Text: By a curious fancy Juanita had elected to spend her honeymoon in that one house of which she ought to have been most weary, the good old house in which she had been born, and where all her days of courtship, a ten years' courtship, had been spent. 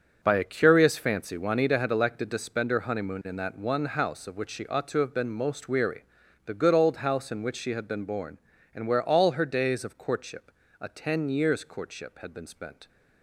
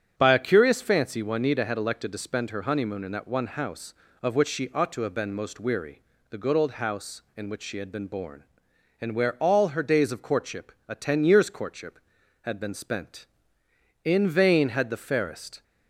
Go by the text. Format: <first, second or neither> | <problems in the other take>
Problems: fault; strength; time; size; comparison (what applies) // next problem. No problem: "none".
first | starts louder than the rest; strong; until 1.1 s; 8 dB; also in the first // goes on to say "In vain had the fairest"; from 14.0 s on; 1.5 s long